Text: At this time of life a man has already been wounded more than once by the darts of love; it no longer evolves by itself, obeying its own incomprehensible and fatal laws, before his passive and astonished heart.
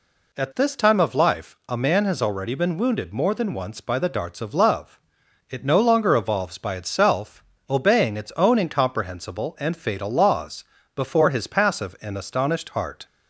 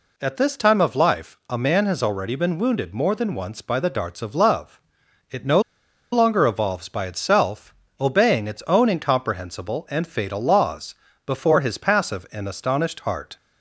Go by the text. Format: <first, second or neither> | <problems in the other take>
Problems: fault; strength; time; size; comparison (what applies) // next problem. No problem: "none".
first | pauses between "no" and "longer"; noticeable; at 5.6 s; 0.52 s long